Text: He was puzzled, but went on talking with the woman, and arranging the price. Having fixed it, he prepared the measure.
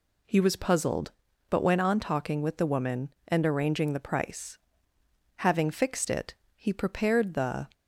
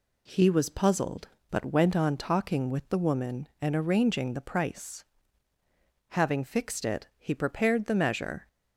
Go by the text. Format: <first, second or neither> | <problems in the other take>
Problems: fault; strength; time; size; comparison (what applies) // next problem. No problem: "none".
second | stops before "measure"; at 7.7 s